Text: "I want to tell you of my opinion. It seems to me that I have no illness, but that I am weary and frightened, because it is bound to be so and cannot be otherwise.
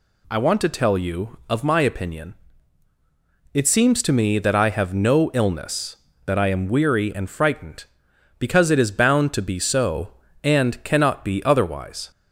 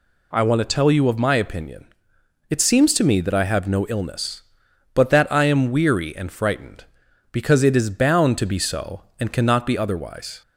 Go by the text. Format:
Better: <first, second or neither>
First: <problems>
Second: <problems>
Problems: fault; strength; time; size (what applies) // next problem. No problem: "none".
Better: second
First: skips "but"; at 6.1 s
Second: none